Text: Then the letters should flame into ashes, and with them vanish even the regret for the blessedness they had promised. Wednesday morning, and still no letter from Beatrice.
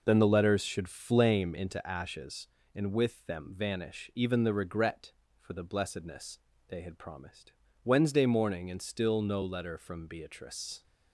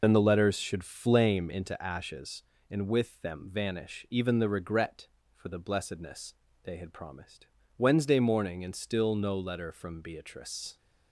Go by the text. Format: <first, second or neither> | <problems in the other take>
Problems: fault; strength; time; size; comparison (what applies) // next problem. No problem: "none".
first | loses the start of "Then"; at 0.0 s; 40 ms // pauses between "blessedness" and "they"; slight; at 6.3 s; 0.30 s long; slight in the first